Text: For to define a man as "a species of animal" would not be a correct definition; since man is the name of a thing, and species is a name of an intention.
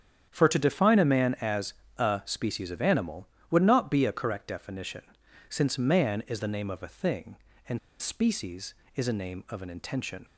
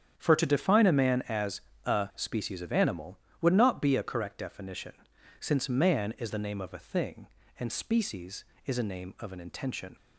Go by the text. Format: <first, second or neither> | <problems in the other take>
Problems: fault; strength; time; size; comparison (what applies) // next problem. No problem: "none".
second | starts louder than the rest; strong; until 1.3 s; 8.5 dB; strong in the second // pauses between "as" and "a"; slight; at 1.7 s; 0.24 s long; slight in the second // pauses between "and" and "species"; slight; at 7.7 s; 0.21 s long